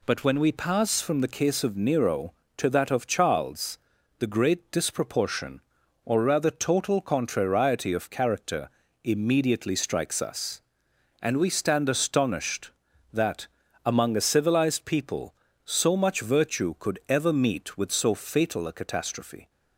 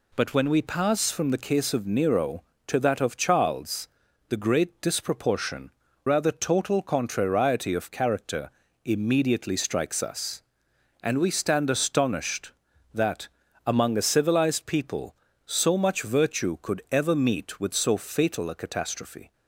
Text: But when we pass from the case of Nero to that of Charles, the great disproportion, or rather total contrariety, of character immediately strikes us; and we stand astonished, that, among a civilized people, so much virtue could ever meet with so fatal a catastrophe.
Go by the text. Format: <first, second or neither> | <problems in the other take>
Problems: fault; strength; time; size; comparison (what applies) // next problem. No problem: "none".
first | skips "or"; at 5.8 s // pauses between "character" and "immediately"; slight; at 8.5 s; 0.34 s long; slight in the first